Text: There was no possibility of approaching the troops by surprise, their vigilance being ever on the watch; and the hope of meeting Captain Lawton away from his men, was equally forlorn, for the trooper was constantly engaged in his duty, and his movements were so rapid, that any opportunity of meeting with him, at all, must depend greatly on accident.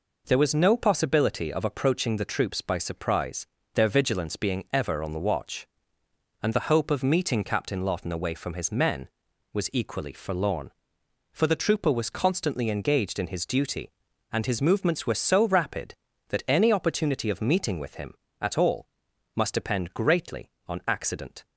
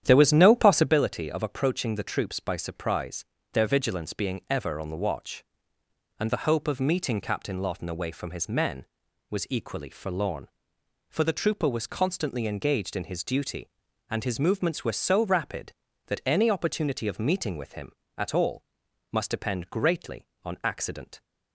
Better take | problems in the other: first | starts louder than the rest; strong; until 1.0 s; 10 dB

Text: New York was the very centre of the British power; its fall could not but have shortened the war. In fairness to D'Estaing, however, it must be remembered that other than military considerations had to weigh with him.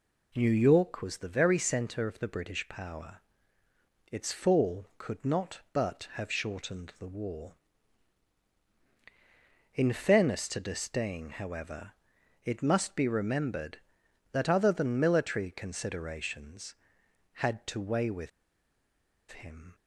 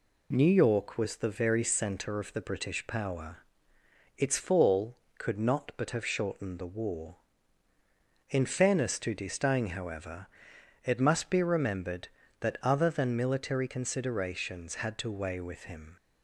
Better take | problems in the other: second | pauses between "with" and "him"; at 18.2 s; 1.0 s long

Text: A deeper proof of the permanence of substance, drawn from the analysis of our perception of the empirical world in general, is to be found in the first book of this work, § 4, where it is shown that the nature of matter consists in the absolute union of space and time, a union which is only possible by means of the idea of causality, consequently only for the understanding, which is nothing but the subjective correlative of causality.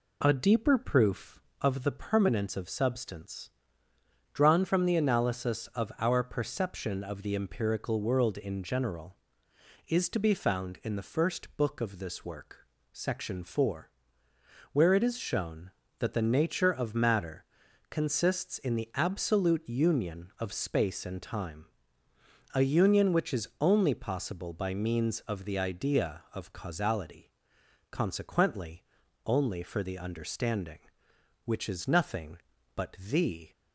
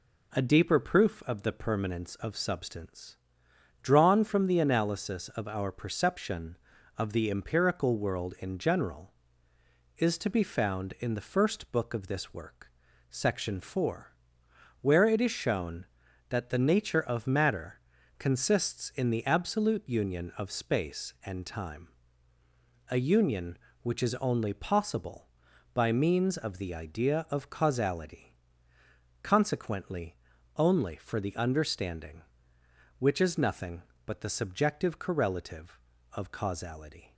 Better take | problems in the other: second | pauses between "matter" and "consists"; noticeable; at 17.4 s; 0.46 s long; also in the second // pauses between "consequently" and "only"; at 28.8 s; 0.40 s long; also in the second // pauses between "but" and "the"; slight; at 32.9 s; 0.16 s long // stops before "subjective correlative of causality"; at 33.5 s

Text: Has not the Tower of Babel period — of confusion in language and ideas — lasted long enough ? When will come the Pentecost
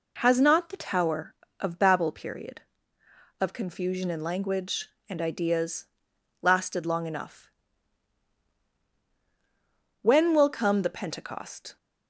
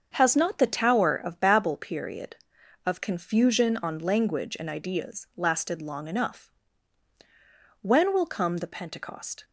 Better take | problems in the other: first | starts louder than the rest; until 1.1 s; 7 dB // says "on" for "in"; at 3.7 s

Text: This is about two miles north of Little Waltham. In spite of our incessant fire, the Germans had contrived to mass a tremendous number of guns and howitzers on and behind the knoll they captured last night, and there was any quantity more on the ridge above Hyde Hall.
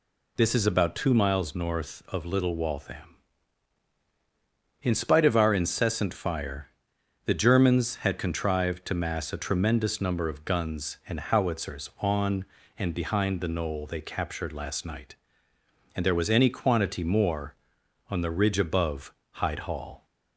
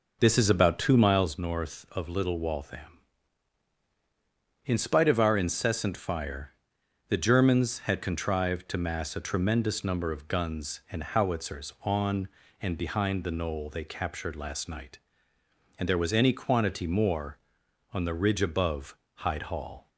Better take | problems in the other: first | starts louder than the rest; noticeable; until 1.4 s; 4.5 dB // pauses between "above" and "Hyde"; slight; at 18.9 s; 0.20 s long; slight in the first

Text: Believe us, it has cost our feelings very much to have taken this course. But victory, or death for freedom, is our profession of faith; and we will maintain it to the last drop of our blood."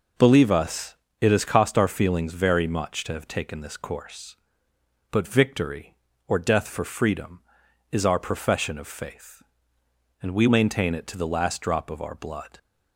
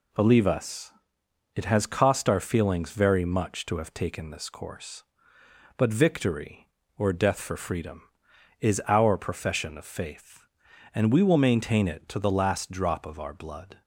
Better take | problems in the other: second | skips "will"; at 10.4 s

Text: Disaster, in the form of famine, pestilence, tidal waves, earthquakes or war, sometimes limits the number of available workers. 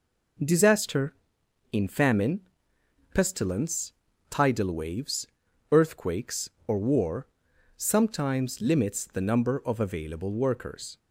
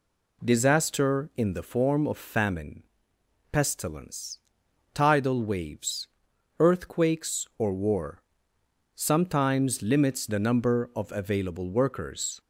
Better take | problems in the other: second | skips "the form of"; at 1.8 s

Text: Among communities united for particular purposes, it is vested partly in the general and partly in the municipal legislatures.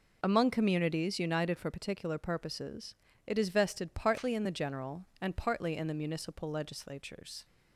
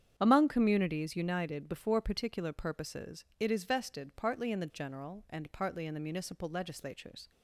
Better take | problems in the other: first | starts louder than the rest; strong; until 1.1 s; 8.5 dB // says "before" for "for"; at 1.6 s

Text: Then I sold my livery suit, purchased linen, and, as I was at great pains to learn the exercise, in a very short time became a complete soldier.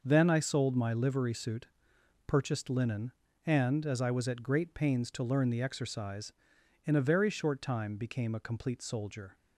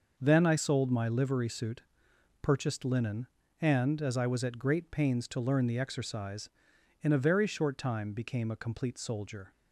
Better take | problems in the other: neither | none

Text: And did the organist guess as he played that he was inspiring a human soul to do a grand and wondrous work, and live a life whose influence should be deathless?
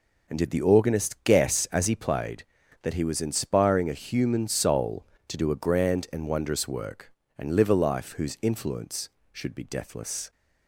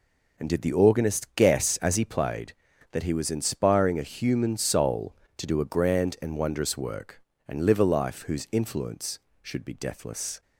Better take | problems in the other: neither | none

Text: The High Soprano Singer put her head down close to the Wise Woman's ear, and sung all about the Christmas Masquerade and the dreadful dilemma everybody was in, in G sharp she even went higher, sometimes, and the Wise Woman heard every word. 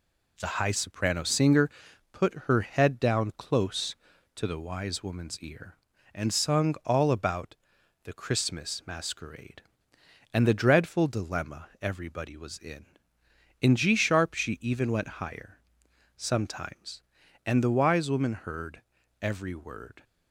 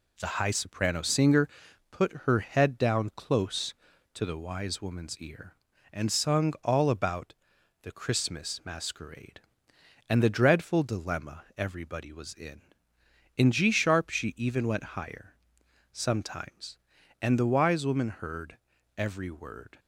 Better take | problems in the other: neither | pauses between "Singer" and "put"; the same in both // pauses between "about" and "the"; noticeable; the same in both // pauses between "heard" and "every"; the same in both

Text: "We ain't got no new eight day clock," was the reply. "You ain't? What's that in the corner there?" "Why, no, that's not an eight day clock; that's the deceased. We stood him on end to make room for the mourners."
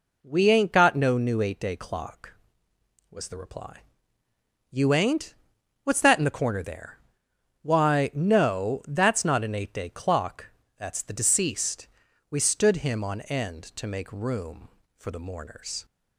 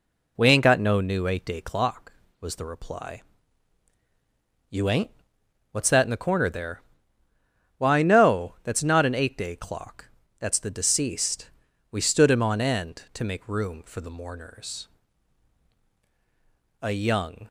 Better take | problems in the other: first | goes on to say "A young"; noticeable; from 16.8 s on; 0.66 s long

